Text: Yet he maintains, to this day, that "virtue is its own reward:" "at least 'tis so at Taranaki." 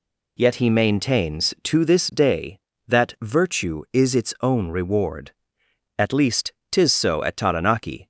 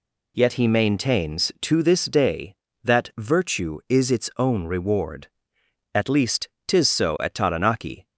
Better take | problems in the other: neither | pauses between "least" and "tis"; slight; the same in both

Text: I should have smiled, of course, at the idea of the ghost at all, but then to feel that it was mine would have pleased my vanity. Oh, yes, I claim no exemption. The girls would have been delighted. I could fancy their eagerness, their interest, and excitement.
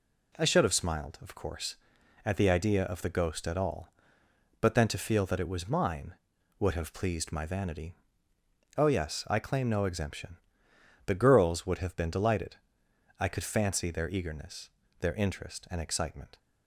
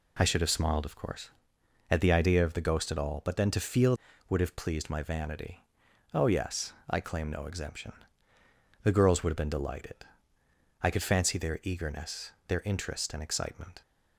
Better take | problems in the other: first | skips "that it was mine"; at 4.1 s

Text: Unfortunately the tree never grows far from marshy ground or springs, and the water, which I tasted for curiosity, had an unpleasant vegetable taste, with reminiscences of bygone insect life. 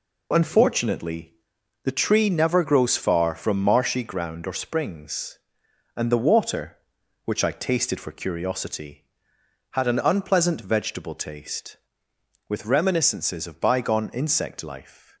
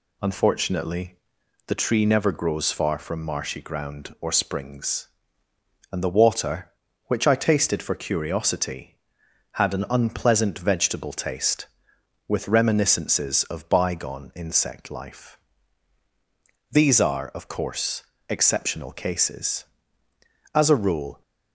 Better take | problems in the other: first | pauses between "Unfortunately" and "the"; noticeable; at 1.1 s; 0.52 s long; noticeable in the first // goes on to say "These are of course exceptional cases as a rule"; strong; from 16.7 s on; 4.5 s long

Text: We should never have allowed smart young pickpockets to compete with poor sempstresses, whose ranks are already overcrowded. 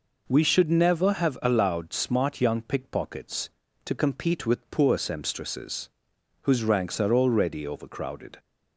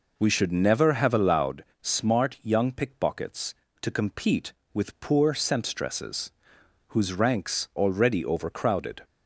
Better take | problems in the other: first | pauses between "allowed" and "smart"; slight; at 1.6 s; 0.16 s long // skips "are"; at 7.7 s

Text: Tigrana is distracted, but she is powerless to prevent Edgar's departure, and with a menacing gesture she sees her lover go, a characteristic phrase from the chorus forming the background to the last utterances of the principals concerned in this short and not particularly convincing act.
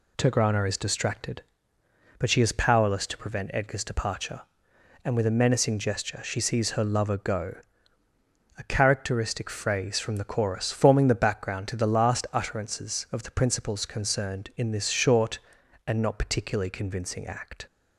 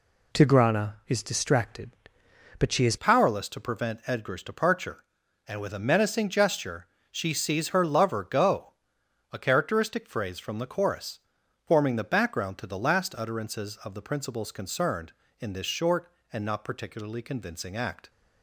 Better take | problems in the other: first | changes voice at "powerless"; from 2.9 s on; 15.1 s long // pauses between "gesture" and "she"; slight; at 6.8 s; 0.24 s long // pauses between "chorus" and "forming"; at 11.1 s; 0.44 s long

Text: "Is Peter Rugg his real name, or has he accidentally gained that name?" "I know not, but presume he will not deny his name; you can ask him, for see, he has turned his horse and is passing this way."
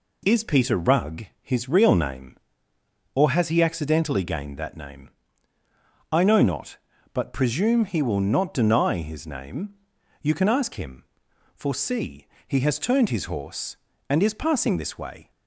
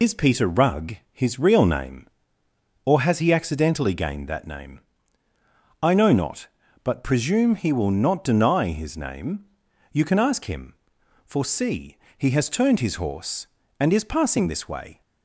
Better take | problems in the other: first | loses the start of "Is"; at 0.0 s; 75 ms // pauses between "Rugg" and "his"; slight; at 0.9 s; 0.16 s long; slight in the first

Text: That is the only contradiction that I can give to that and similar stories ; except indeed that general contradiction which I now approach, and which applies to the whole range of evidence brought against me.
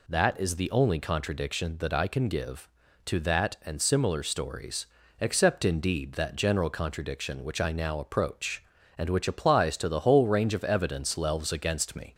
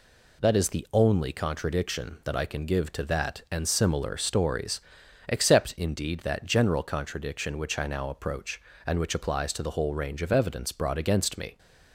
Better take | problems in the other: second | says "lelves" for "brought"; at 11.1 s

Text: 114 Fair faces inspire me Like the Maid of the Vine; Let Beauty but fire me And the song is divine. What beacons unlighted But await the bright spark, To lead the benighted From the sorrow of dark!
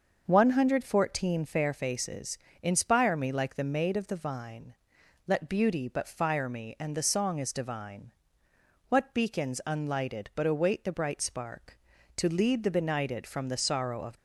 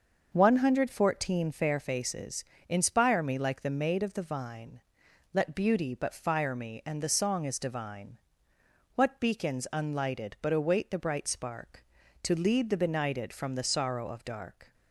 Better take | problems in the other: second | starts louder than the rest; until 1.2 s; 6.5 dB; also in the second // pauses between "faces" and "inspire"; slight; at 2.3 s; 0.24 s long; slight in the second // stops before "dark"; at 14.1 s

